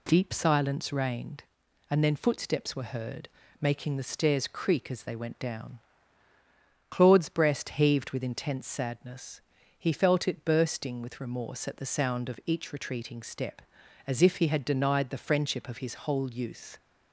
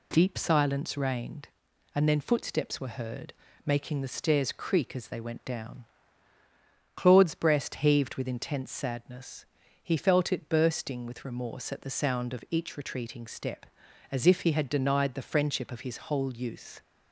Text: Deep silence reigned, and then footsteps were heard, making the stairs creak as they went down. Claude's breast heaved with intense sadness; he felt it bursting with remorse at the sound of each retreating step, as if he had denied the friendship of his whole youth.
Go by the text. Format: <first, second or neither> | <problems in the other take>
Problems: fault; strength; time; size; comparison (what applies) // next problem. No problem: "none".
neither | none